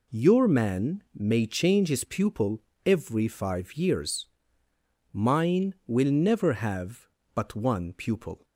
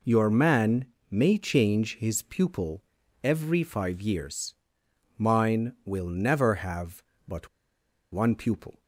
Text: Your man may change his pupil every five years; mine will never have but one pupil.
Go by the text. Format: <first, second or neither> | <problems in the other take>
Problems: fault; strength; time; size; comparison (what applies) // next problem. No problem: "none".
first | pauses between "man" and "may"; slight; at 0.8 s; 0.26 s long // pauses between "pupil" and "every"; at 2.8 s; 0.42 s long; slight in the first // pauses between "but" and "one"; noticeable; at 7.4 s; 0.64 s long